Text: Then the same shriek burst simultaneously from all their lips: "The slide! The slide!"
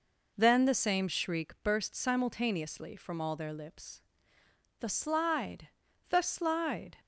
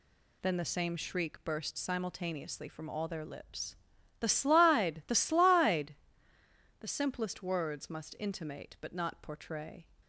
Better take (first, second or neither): first